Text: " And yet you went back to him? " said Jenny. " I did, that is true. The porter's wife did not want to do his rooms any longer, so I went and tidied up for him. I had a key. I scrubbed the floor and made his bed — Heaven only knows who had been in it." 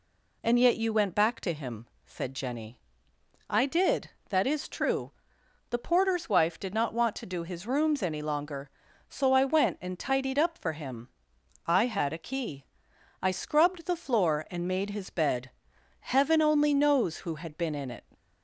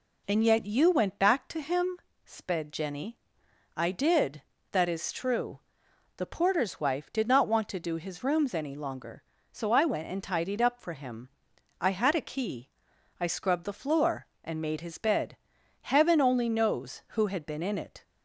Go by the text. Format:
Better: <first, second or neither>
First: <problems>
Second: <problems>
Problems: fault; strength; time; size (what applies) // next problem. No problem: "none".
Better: first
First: none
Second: says "sped" for "said"; at 2.2 s